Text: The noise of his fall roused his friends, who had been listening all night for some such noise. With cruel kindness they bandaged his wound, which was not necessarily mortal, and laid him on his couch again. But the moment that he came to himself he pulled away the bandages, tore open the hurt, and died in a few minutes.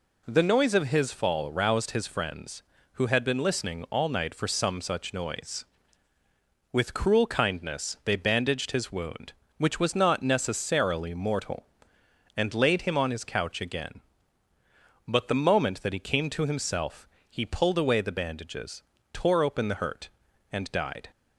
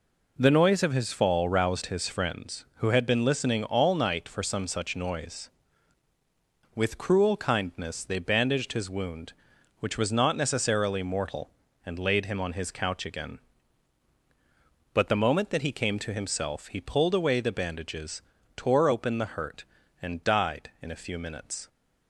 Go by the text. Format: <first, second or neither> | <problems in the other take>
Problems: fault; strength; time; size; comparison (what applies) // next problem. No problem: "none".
second | pauses between "himself" and "he"; slight; at 17.0 s; 0.24 s long // stops before "in a few minutes"; at 21.1 s